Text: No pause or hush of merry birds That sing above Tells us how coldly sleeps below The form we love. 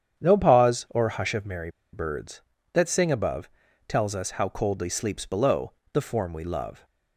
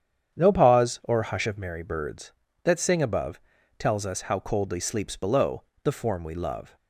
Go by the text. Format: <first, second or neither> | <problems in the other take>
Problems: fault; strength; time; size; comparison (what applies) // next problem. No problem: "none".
second | starts louder than the rest; strong; until 1.2 s; 8.5 dB; strong in the second // pauses between "merry" and "birds"; slight; at 1.6 s; 0.23 s long // pauses between "above" and "Tells"; at 3.4 s; 0.40 s long; also in the second // pauses between "below" and "The"; slight; at 5.7 s; 0.20 s long; slight in the second